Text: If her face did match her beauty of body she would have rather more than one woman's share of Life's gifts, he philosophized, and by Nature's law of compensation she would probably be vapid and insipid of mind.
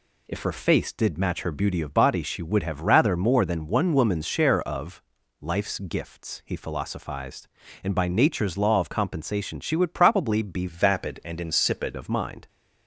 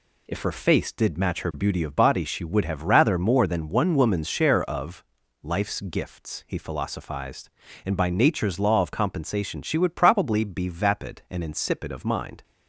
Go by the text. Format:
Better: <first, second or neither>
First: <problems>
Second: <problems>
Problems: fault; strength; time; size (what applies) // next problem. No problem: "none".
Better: second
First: pauses between "of" and "Life's"; at 5.0 s; 0.38 s long // changes voice from "vapid" to "insipid"; from 10.6 to 11.9 s; 1.3 s long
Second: pauses between "of" and "Life's"; at 5.0 s; 0.38 s long